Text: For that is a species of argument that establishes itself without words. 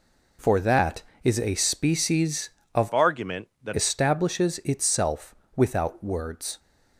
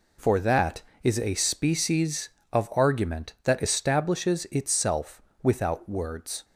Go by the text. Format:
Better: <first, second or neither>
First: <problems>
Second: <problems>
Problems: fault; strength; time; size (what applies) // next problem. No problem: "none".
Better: second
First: changes voice from "argument" to "that"; from 2.9 to 3.7 s; 0.8 s long // pauses between "itself" and "without"; slight; at 5.3 s; 0.22 s long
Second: pauses between "itself" and "without"; slight; at 5.2 s; 0.22 s long